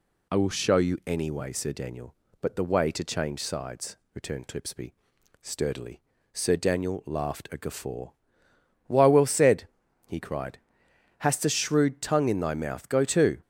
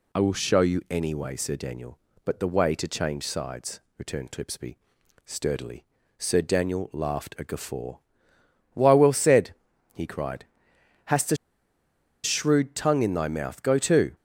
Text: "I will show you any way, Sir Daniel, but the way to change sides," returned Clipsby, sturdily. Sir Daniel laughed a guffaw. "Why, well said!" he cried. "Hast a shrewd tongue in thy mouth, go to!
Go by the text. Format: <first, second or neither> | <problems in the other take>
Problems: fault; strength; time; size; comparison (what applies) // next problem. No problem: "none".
first | pauses between "a" and "shrewd"; noticeable; at 11.3 s; 0.87 s long